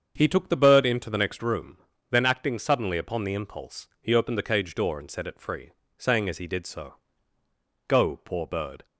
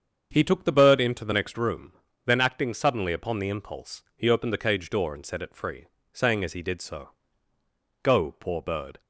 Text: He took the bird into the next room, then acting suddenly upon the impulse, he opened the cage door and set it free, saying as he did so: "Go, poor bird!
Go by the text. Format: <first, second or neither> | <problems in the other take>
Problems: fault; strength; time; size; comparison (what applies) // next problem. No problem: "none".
neither | starts louder than the rest; the same in both